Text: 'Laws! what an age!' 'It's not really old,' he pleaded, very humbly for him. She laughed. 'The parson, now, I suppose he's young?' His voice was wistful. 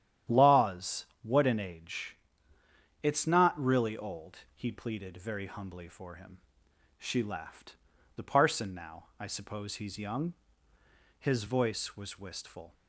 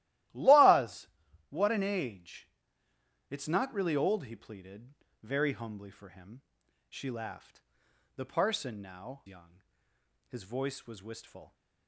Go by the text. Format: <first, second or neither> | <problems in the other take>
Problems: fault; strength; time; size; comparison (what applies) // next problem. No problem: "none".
first | starts louder than the rest; strong; until 1.7 s; 15 dB; strong in the first // skips "I suppose he's"; at 9.2 s